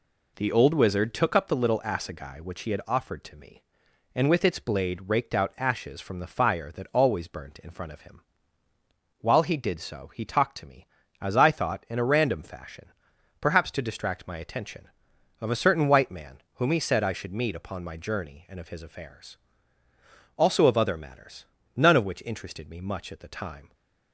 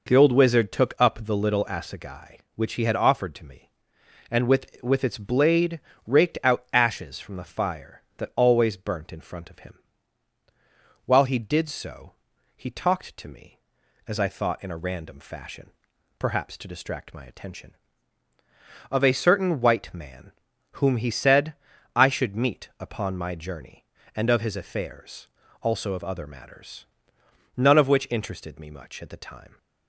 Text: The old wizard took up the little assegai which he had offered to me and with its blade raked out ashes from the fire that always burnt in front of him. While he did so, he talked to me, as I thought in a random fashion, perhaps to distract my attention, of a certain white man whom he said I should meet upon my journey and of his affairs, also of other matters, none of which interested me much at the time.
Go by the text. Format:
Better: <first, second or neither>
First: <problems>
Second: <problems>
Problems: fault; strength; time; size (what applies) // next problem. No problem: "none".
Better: first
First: pauses between "man" and "whom"; slight; at 16.3 s; 0.18 s long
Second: says "with" twice; at 4.8 s // pauses between "blade" and "raked"; slight; at 5.8 s; 0.24 s long // pauses between "man" and "whom"; noticeable; at 20.3 s; 0.48 s long // pauses between "said" and "I"; at 21.5 s; 0.42 s long